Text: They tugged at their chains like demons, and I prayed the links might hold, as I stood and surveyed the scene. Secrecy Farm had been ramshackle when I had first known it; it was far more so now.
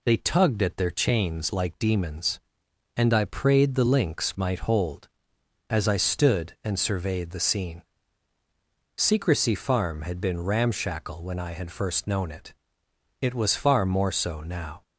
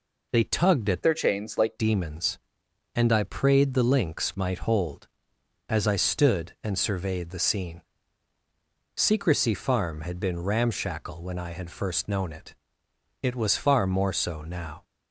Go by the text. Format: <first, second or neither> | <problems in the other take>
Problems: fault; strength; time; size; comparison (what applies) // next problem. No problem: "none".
first | changes voice from "their" to "like"; from 1.0 to 1.7 s; 0.7 s long